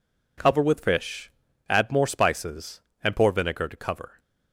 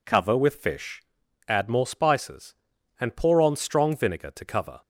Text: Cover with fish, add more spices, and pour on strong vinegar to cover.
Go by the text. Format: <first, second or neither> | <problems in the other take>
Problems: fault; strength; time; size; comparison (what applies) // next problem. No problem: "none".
second | skips "on strong"; at 3.3 s